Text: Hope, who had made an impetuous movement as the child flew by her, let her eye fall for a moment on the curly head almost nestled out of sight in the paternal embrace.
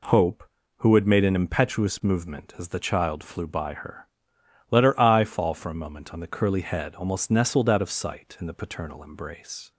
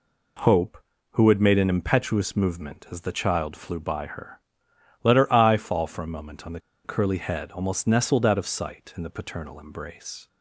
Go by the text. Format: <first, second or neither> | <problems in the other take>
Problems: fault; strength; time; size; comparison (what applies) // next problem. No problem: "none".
first | pauses between "the" and "curly"; slight; at 6.5 s; 0.24 s long